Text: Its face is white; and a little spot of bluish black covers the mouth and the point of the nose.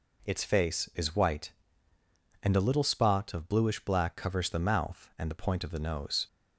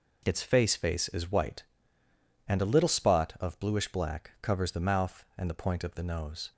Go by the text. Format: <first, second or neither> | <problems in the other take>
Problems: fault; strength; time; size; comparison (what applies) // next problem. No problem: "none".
first | says "face" twice; at 0.7 s